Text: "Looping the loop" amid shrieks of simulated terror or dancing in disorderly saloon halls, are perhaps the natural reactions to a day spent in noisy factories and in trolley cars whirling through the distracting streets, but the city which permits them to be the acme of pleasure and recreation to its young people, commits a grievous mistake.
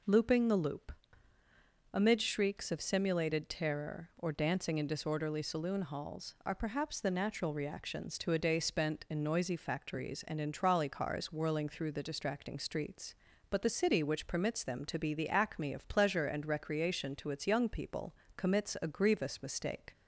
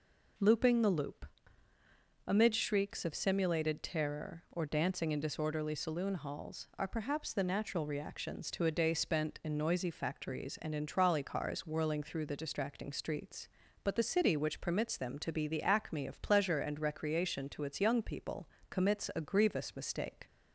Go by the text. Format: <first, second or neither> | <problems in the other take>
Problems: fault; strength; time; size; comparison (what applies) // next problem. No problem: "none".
neither | pauses between "loop" and "amid"; the same in both